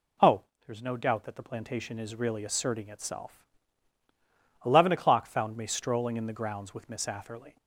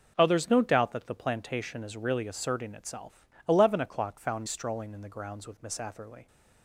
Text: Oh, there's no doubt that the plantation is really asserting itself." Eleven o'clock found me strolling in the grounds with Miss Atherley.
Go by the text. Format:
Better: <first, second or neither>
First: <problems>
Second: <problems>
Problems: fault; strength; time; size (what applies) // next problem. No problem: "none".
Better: first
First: none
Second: skips "me"; at 4.4 s